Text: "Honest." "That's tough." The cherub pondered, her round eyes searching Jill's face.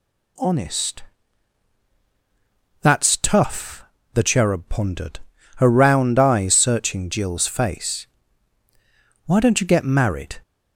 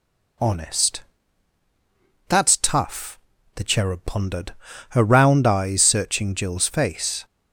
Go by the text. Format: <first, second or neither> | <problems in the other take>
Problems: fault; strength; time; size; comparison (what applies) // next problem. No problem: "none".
second | goes on to say "Why don't you get married"; noticeable; from 9.2 s on; 1.1 s long